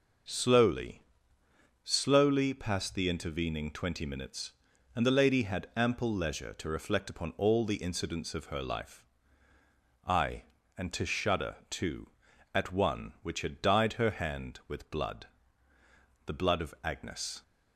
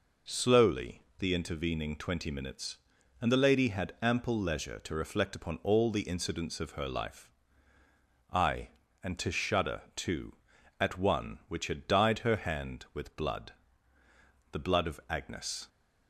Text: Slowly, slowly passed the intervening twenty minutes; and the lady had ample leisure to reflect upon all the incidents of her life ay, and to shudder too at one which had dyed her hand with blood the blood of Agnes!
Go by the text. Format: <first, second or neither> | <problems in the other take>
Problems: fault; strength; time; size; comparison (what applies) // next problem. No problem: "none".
first | skips "slowly passed"; at 1.1 s // pauses between "life" and "ay"; at 7.2 s; 1.0 s long; also in the first // pauses between "shudder" and "too"; slight; at 9.7 s; 0.16 s long; slight in the first // pauses between "blood" and "the"; noticeable; at 13.5 s; 0.98 s long; noticeable in the first